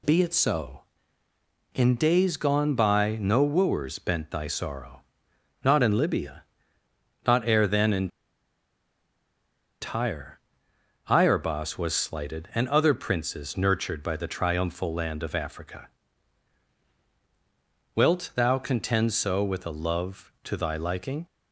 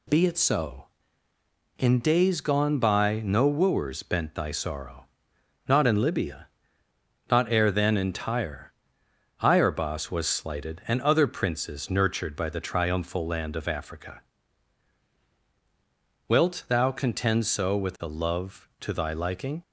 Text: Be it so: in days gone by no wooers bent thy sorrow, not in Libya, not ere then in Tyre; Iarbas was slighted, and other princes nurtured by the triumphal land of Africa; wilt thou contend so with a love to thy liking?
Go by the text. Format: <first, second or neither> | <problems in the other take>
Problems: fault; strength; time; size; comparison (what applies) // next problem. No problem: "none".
second | pauses between "in" and "Tyre"; strong; at 8.1 s; 1.7 s long